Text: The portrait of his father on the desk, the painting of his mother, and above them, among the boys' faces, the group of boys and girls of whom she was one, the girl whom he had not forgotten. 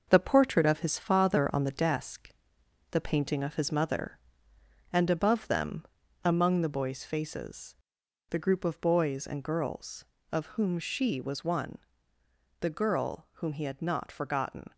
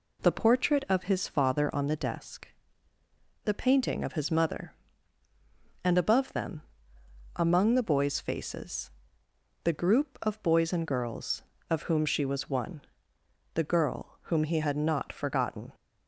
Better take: second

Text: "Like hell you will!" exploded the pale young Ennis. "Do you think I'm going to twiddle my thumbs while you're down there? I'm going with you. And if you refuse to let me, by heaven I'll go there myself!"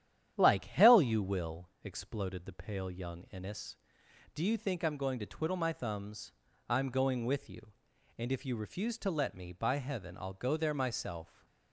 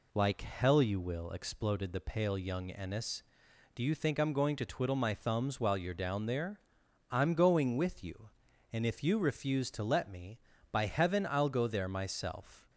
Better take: second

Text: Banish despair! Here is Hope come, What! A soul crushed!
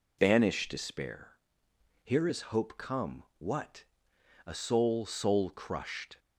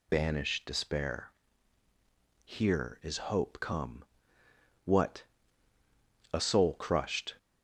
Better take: second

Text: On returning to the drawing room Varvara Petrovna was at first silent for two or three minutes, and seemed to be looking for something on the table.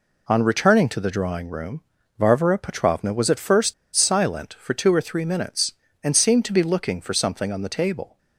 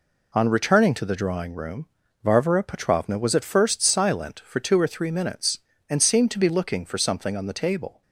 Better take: second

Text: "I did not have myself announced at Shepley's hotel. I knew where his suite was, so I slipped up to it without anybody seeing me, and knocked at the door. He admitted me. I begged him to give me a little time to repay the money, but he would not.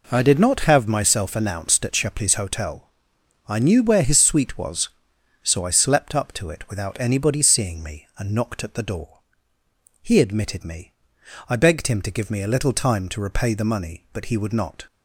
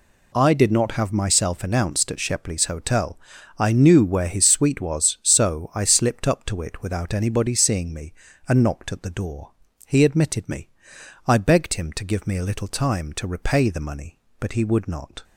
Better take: second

